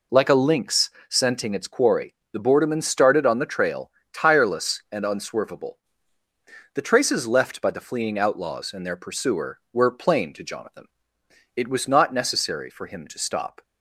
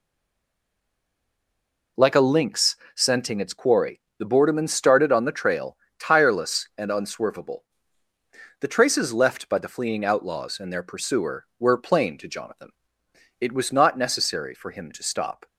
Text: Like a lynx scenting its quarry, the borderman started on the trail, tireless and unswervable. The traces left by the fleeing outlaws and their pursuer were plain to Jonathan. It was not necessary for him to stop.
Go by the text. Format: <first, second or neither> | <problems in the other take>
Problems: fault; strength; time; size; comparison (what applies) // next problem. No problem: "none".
first | stays silent before the first word; noticeable; until 1.9 s; 1.9 s long // pauses between "lynx" and "scenting"; slight; at 2.7 s; 0.18 s long; slight in the first